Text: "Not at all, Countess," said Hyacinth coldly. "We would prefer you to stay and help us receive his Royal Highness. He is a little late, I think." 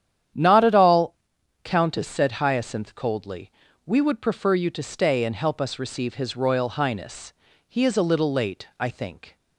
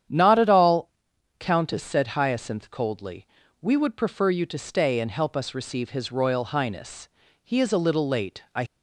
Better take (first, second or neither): first